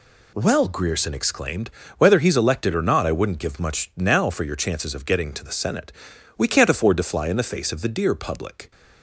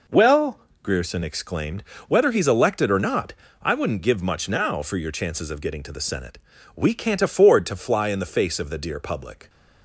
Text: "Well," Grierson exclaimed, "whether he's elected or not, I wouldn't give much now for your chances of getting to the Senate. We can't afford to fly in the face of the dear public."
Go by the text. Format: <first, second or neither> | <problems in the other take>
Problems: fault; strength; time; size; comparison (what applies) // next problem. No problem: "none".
neither | none